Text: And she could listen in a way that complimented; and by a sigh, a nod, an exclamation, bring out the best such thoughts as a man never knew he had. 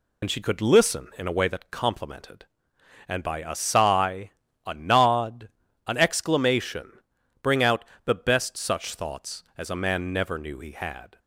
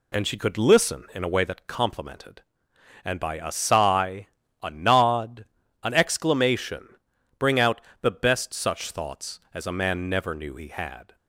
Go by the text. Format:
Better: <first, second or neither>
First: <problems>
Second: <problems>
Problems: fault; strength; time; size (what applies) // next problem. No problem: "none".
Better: second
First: loses the start of "And"; at 0.2 s; 65 ms // pauses between "out" and "the"; slight; at 7.8 s; 0.20 s long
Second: pauses between "out" and "the"; slight; at 7.8 s; 0.20 s long